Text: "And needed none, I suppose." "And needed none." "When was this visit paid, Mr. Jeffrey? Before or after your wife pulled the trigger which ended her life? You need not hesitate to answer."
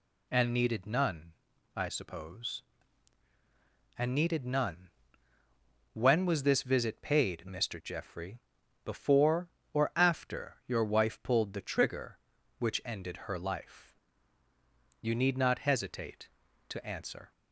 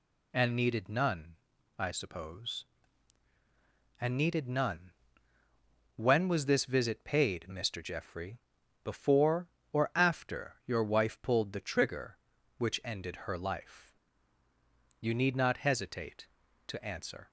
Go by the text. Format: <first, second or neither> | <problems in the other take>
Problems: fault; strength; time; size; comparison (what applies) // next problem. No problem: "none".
neither | none